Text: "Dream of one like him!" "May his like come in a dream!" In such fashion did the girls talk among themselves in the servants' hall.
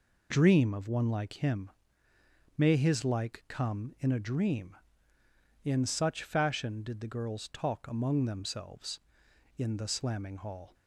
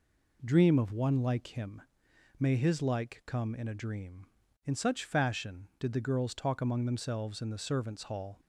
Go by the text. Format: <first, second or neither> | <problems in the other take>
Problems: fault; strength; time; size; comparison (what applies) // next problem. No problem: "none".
second | says "slamming" for "servants"; at 9.8 s